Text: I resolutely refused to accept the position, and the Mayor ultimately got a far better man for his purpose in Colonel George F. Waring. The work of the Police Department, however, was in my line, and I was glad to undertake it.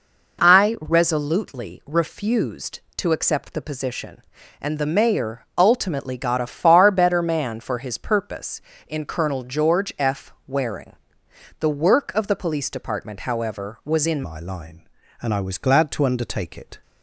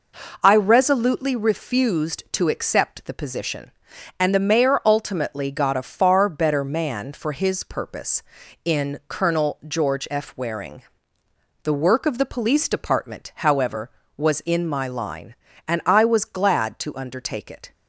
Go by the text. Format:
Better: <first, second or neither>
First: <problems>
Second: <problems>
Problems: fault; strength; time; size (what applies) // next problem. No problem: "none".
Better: second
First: changes voice at "my"; from 14.2 s on; 2.5 s long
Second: none